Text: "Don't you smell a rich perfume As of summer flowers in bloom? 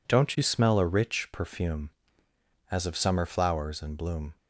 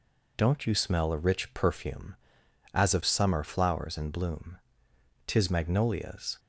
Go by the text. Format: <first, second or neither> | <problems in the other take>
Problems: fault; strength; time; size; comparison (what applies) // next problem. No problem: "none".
first | goes on to say "Tis magnolias"; noticeable; from 5.2 s on; 1.1 s long